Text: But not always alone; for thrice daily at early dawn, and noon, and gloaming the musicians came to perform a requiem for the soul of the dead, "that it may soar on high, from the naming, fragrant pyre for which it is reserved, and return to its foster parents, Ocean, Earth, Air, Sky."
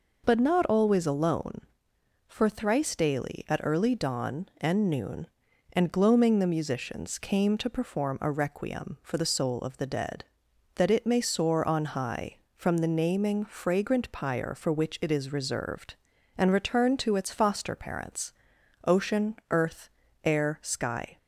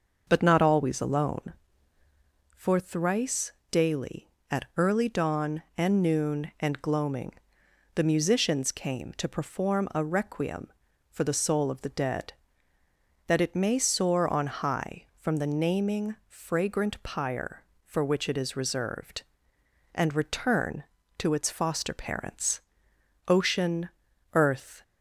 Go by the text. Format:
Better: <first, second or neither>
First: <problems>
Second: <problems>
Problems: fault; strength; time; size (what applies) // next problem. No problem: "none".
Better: first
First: none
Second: starts louder than the rest; until 1.2 s; 6.5 dB // pauses between "thrice" and "daily"; slight; at 3.5 s; 0.18 s long // pauses between "gloaming" and "the"; noticeable; at 7.3 s; 0.60 s long // stops before "Air Sky"; at 24.8 s